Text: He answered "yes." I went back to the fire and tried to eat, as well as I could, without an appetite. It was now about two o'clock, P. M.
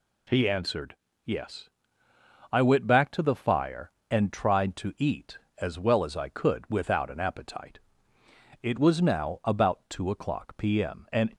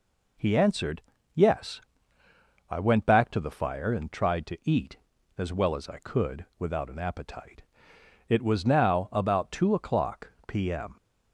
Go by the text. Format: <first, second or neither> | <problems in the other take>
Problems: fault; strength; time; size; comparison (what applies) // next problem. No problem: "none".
second | pauses between "answered" and "yes"; slight; at 0.9 s; 0.30 s long; slight in the second // goes on to say "and"; slight; from 11.1 s on; 0.24 s long